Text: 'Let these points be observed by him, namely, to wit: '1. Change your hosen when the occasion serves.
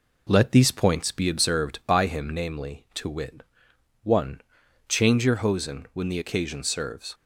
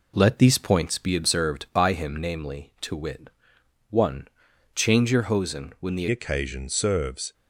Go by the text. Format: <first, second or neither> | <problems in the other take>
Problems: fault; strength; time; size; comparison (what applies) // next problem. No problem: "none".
first | changes voice at "occasion"; from 6.1 s on; 1.2 s long